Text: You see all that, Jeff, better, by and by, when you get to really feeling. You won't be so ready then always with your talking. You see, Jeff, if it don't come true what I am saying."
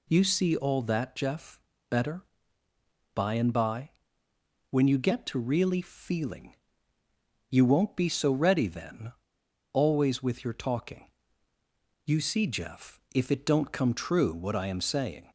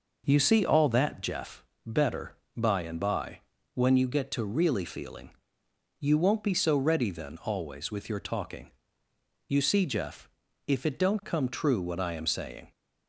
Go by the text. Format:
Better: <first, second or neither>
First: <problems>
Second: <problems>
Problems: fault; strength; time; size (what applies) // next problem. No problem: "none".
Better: second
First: pauses between "then" and "always"; noticeable; at 9.1 s; 0.60 s long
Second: none